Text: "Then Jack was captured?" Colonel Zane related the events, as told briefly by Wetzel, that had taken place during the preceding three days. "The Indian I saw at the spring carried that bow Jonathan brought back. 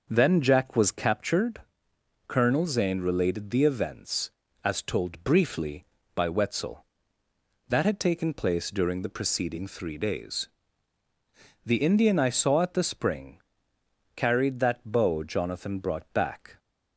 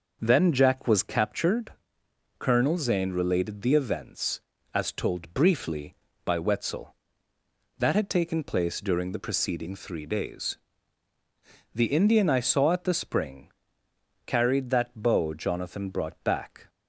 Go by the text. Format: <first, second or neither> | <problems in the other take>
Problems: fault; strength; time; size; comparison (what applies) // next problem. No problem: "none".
neither | pauses between "spring" and "carried"; noticeable; the same in both